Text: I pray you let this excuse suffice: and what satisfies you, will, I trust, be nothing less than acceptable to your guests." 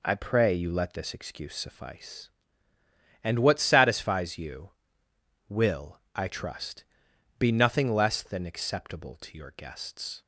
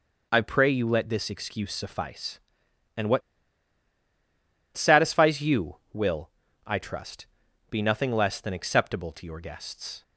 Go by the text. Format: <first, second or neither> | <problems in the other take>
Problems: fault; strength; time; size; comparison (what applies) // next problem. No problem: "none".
first | pauses between "what" and "satisfies"; strong; at 3.2 s; 1.5 s long